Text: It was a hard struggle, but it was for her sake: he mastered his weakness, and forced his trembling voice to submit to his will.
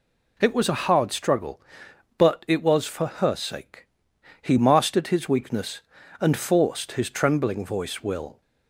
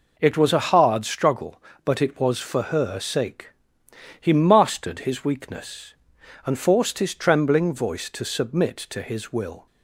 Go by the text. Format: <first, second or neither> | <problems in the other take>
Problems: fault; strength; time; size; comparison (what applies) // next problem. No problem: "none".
second | skips "to submit to his"; at 8.0 s